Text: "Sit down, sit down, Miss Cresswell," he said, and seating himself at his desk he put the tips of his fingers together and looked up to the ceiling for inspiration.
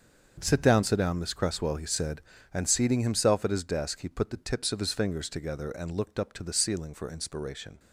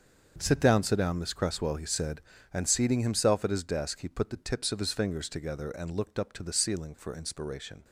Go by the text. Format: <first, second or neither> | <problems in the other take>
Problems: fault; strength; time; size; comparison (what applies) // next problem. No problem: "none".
neither | starts louder than the rest; the same in both